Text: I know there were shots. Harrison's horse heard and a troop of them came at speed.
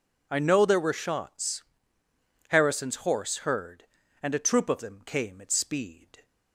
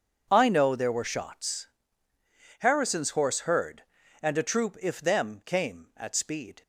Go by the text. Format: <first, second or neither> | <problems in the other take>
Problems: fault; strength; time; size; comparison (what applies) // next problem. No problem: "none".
first | says "if" for "of"; at 4.8 s